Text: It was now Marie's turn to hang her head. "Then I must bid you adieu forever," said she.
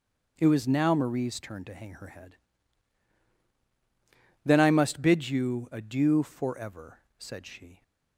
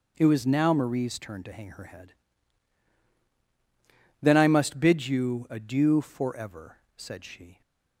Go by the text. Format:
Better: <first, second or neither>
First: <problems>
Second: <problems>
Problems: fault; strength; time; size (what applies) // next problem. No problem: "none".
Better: neither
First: starts louder than the rest; until 1.3 s; 7 dB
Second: starts louder than the rest; until 1.1 s; 7 dB